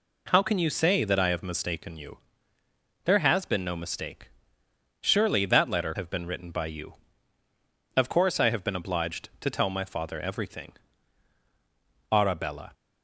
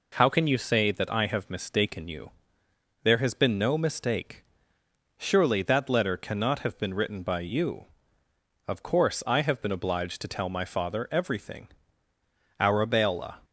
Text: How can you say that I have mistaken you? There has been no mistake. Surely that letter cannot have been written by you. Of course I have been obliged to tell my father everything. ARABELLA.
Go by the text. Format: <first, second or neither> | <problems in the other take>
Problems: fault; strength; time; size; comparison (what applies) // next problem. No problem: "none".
second | skips "cannot"; at 5.9 s